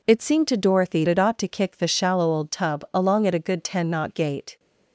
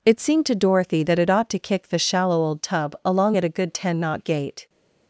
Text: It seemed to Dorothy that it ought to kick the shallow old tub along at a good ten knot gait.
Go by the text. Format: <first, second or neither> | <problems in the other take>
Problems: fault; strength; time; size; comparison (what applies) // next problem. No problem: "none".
second | skips "that"; at 1.0 s